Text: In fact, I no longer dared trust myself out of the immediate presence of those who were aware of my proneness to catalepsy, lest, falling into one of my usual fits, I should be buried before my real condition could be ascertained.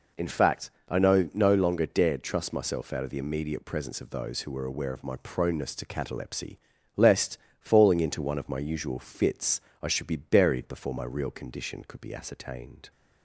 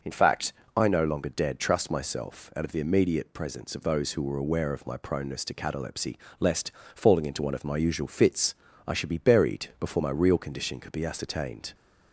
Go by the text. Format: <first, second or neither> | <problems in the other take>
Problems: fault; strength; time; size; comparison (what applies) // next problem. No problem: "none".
second | says "no" twice; at 1.3 s